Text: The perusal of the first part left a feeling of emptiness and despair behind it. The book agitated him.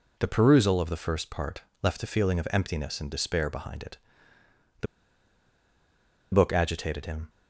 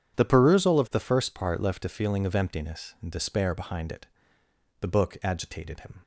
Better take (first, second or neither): second